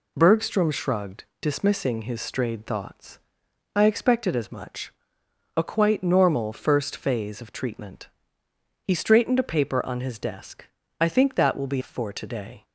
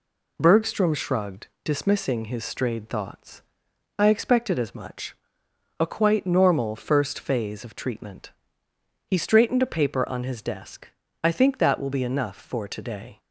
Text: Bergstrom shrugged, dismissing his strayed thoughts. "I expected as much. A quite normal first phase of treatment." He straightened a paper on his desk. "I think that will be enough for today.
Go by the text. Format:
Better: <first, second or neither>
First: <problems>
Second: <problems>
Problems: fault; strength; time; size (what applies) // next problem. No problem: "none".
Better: second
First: skips "enough"; at 11.8 s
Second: none